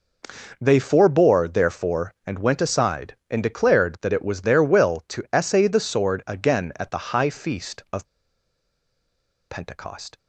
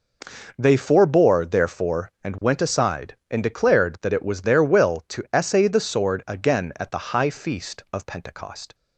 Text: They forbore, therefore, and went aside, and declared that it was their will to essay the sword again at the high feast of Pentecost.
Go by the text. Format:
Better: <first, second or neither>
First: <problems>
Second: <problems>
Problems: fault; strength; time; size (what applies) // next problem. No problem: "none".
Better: second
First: pauses between "of" and "Pentecost"; strong; at 8.0 s; 1.4 s long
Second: none